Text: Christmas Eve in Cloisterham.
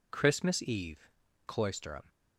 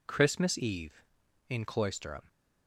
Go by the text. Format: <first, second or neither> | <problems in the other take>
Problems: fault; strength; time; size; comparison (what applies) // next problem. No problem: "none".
second | skips "in"; at 1.2 s